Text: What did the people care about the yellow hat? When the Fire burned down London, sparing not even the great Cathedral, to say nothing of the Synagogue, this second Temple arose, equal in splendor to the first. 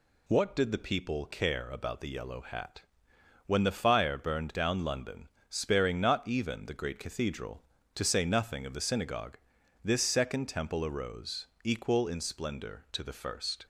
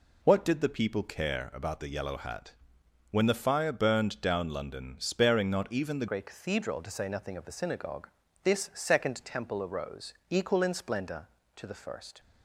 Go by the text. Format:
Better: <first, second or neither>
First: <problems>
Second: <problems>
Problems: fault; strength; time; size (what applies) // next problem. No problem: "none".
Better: first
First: none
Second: changes voice at "great"; from 6.0 s on; 6.1 s long